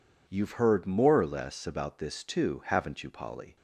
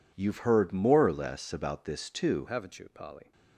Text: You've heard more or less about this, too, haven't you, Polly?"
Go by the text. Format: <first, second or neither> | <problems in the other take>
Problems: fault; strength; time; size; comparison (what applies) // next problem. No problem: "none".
first | changes voice at "haven't"; from 2.4 s on; 0.9 s long